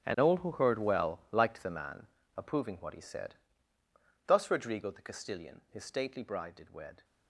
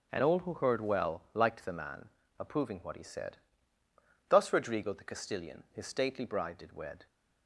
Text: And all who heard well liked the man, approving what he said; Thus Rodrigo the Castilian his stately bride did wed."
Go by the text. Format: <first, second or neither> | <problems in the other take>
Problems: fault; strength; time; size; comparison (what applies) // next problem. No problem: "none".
second | gets quieter; strong; throughout; 15.5 dB // starts louder than the rest; strong; until 1.1 s; 10 dB; also in the second